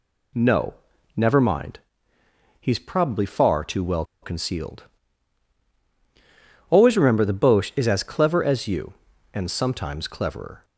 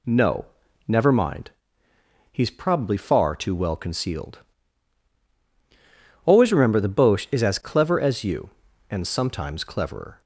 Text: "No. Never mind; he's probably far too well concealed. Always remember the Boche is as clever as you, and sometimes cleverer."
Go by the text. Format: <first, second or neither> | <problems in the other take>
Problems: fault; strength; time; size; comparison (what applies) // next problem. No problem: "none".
second | pauses between "well" and "concealed"; slight; at 4.0 s; 0.18 s long